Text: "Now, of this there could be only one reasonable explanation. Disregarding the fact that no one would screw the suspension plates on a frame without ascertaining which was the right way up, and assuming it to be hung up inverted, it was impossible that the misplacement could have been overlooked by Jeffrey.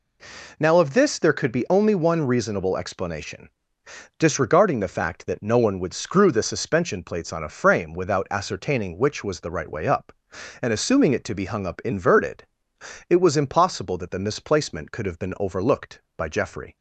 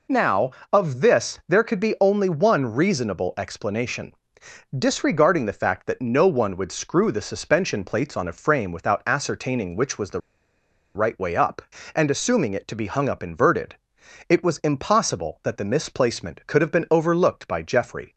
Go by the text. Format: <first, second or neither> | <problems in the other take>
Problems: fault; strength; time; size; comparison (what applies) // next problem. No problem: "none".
first | pauses between "the" and "right"; noticeable; at 10.1 s; 0.75 s long